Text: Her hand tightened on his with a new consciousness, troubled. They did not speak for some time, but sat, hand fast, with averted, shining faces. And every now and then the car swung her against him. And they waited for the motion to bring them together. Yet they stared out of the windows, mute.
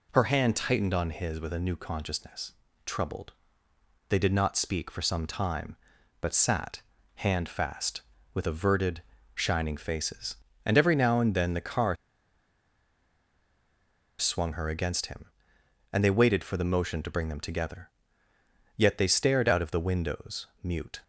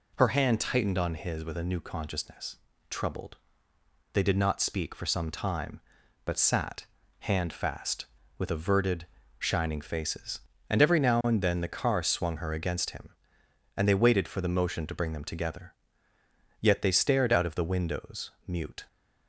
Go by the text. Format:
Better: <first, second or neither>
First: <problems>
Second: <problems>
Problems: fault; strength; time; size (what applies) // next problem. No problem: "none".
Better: second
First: pauses between "car" and "swung"; strong; at 11.9 s; 2.2 s long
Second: none